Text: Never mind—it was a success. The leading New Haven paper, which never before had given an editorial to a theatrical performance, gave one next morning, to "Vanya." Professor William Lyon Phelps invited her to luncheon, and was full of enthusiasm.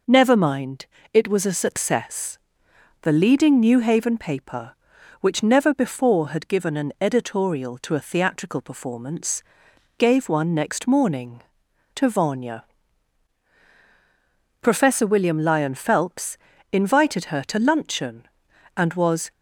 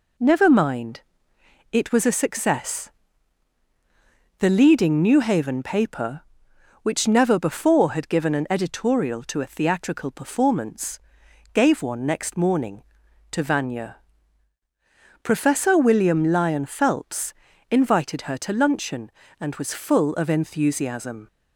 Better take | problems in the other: second | pauses between "Phelps" and "invited"; slight; at 16.3 s; 0.36 s long; slight in the second // stops before "full of enthusiasm"; at 19.3 s

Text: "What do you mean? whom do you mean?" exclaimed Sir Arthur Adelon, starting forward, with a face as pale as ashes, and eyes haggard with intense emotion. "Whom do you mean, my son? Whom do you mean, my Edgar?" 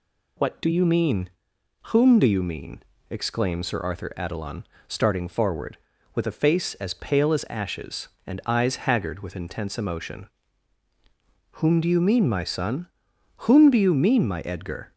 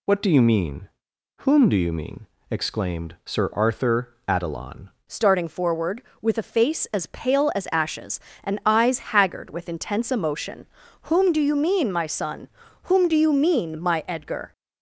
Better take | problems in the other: first | changes voice at "starting"; from 5.0 s on; 9.5 s long

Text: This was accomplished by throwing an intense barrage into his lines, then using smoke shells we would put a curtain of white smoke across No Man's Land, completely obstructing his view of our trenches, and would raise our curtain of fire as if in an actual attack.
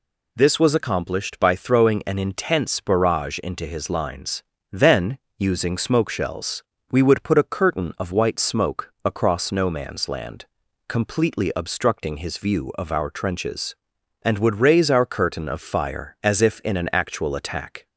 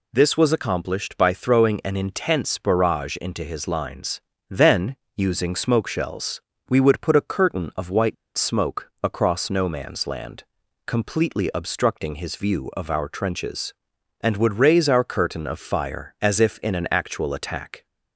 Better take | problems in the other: first | pauses between "then" and "using"; slight; at 4.9 s; 0.18 s long; slight in the first // pauses between "shells" and "we"; slight; at 6.4 s; 0.28 s long; slight in the first // pauses between "white" and "smoke"; slight; at 8.1 s; 0.22 s long

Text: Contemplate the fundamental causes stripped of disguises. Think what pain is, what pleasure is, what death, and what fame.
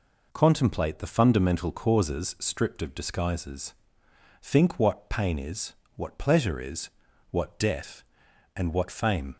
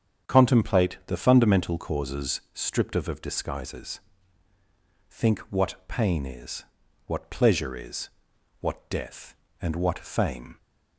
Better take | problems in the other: first | starts louder than the rest; strong; until 1.3 s; 7.5 dB // says "of" twice; at 3.0 s

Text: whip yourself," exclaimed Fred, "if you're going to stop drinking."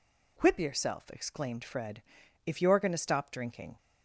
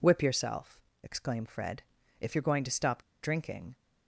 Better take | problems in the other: first | pauses between "stop" and "drinking"; slight; at 3.0 s; 0.19 s long

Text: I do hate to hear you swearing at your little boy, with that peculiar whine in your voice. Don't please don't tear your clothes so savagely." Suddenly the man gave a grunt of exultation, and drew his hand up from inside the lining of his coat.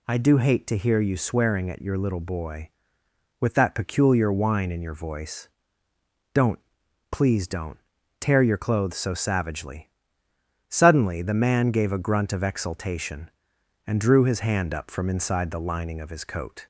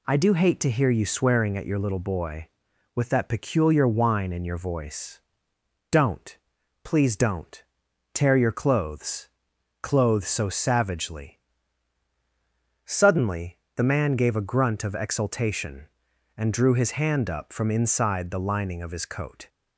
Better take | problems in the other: first | pauses between "Don't" and "please"; noticeable; at 6.3 s; 0.46 s long; noticeable in the first // pauses between "don't" and "tear"; noticeable; at 7.6 s; 0.50 s long; also in the first // says "clothes" twice; at 9.8 s // pauses between "Suddenly" and "the"; slight; at 13.5 s; 0.20 s long

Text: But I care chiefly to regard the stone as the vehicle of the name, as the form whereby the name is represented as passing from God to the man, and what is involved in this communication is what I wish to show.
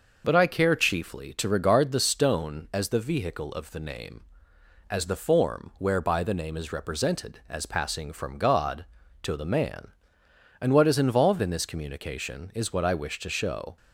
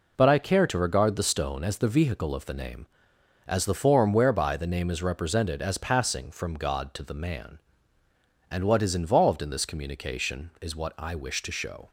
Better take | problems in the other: first | skips "chiefly"; at 0.6 s

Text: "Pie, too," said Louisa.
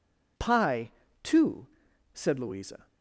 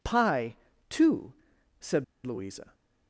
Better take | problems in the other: first | pauses between "said" and "Louisa"; slight; at 2.0 s; 0.21 s long

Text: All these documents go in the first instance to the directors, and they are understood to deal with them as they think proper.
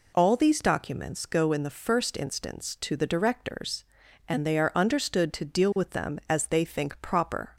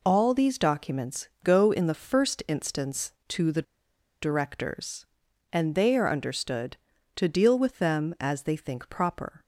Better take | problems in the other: first | pauses between "documents" and "go"; slight; at 1.2 s; 0.16 s long // pauses between "the" and "directors"; noticeable; at 3.6 s; 0.59 s long

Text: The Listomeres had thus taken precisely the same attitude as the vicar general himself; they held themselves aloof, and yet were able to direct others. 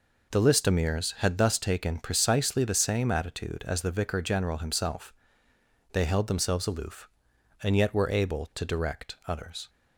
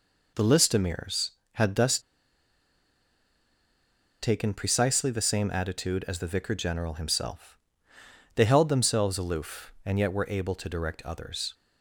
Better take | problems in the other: first | pauses between "thus" and "taken"; strong; at 1.9 s; 2.2 s long

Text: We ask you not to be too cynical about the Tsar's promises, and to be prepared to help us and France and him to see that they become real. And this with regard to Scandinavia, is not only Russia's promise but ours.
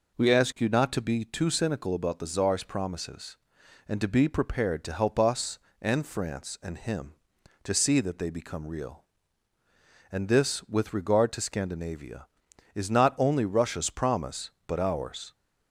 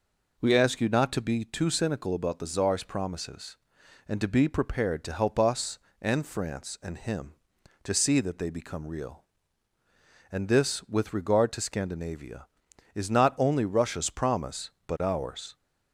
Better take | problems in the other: neither | none

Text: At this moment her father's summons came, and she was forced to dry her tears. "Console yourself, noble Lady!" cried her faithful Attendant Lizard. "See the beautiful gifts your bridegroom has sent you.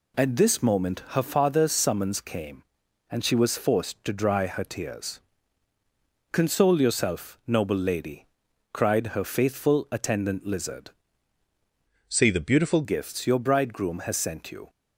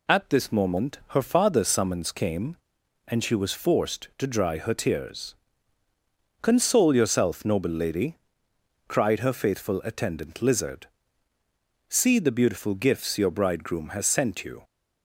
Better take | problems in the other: second | changes voice from "See" to "beautiful"; from 12.0 to 12.8 s; 0.8 s long

